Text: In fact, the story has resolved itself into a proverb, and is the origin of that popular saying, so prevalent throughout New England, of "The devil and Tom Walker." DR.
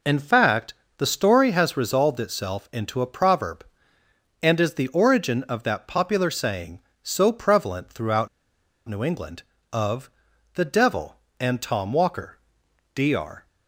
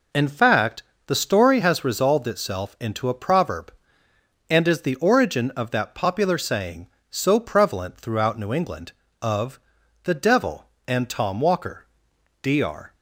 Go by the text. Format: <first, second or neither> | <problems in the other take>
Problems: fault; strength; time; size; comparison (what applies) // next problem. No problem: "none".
second | pauses between "throughout" and "New"; noticeable; at 8.2 s; 0.60 s long // pauses between "of" and "The"; noticeable; at 10.0 s; 0.46 s long; noticeable in the second